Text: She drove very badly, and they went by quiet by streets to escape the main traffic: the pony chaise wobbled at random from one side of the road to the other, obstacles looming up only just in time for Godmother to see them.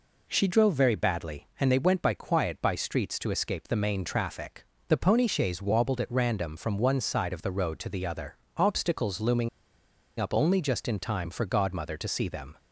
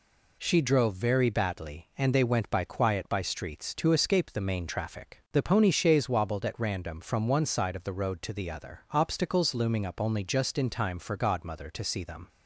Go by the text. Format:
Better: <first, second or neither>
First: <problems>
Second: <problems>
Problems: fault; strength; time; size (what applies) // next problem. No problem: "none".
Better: second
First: pauses between "looming" and "up"; noticeable; at 9.4 s; 0.70 s long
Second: none